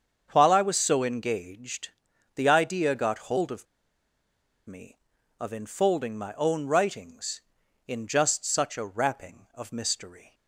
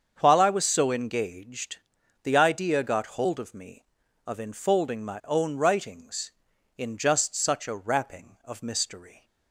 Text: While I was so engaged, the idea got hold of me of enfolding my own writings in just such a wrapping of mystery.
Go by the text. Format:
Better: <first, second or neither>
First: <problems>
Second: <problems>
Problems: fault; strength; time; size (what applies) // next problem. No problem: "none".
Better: second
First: starts louder than the rest; until 1.3 s; 7 dB // pauses between "of" and "me"; at 3.6 s; 1.0 s long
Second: starts louder than the rest; until 1.2 s; 7 dB